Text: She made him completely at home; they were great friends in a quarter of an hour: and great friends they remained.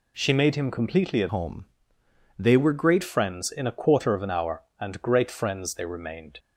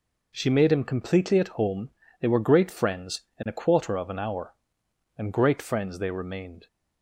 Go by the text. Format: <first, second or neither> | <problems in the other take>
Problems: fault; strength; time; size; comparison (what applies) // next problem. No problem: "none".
second | changes voice from "home" to "great"; from 1.2 to 3.0 s; 1.8 s long